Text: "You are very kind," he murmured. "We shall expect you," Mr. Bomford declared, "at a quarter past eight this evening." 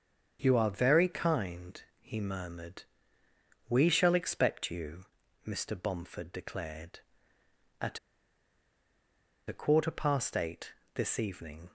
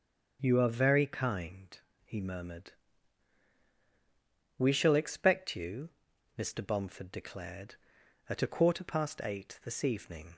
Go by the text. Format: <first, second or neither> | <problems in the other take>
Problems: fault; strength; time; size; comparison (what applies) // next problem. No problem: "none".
second | starts louder than the rest; strong; until 1.4 s; 7.5 dB; also in the second // pauses between "at" and "a"; strong; at 7.9 s; 1.4 s long // pauses between "eight" and "this"; slight; at 10.7 s; 0.20 s long